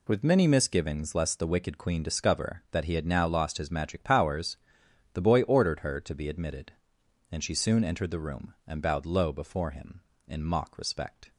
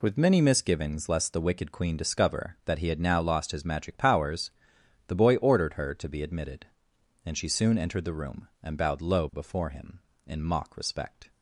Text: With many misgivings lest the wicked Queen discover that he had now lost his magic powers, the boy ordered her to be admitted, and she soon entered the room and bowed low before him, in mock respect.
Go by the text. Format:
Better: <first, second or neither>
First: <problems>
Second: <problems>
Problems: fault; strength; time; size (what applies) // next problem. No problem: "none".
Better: neither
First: none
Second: none